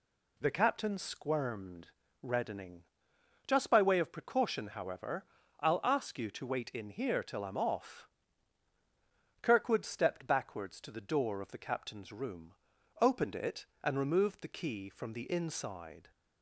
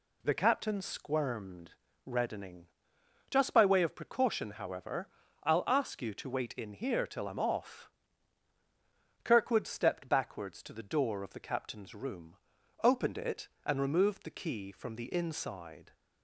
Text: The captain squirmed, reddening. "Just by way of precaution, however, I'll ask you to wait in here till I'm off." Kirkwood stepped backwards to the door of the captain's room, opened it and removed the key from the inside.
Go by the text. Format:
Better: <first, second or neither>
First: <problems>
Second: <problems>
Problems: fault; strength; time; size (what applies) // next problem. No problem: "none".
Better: neither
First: none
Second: none